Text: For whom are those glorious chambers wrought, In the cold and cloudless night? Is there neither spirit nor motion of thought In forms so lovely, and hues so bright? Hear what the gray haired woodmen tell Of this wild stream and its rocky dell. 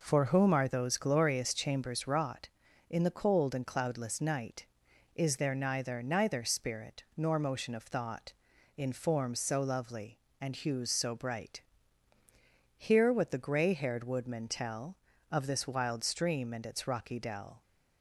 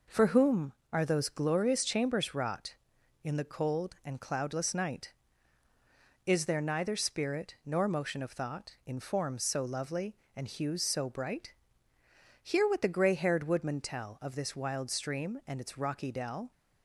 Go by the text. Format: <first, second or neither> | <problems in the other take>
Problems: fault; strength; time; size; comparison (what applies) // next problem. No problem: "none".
second | says "neither" twice; at 6.0 s